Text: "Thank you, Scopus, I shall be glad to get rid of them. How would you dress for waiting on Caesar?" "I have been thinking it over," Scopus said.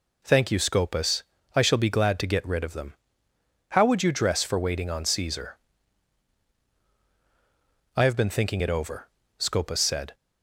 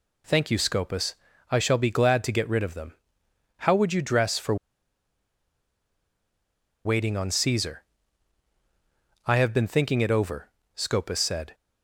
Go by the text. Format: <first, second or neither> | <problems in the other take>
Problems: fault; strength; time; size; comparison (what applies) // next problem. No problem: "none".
first | pauses between "for" and "waiting"; strong; at 4.5 s; 2.2 s long